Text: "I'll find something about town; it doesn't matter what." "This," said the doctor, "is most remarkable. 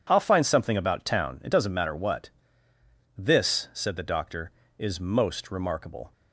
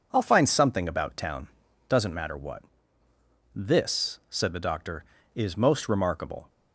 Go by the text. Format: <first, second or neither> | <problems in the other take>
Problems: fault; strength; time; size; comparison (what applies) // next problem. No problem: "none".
first | skips "it"; at 1.6 s